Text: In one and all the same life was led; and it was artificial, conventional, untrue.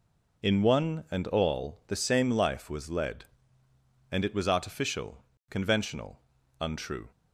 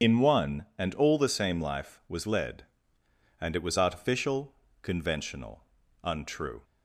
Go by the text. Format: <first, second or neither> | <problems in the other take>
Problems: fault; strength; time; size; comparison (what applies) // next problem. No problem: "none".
first | loses the start of "In"; at 0.0 s; 55 ms